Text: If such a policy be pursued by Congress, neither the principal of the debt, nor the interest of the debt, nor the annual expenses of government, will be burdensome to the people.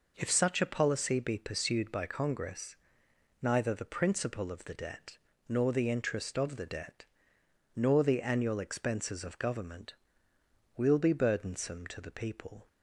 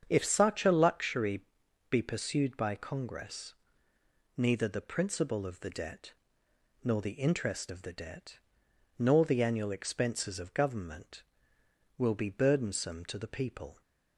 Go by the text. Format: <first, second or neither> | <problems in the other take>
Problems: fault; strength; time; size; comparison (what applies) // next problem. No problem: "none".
first | starts louder than the rest; strong; until 1.1 s; 7.5 dB // says "luxury" for "policy"; at 0.7 s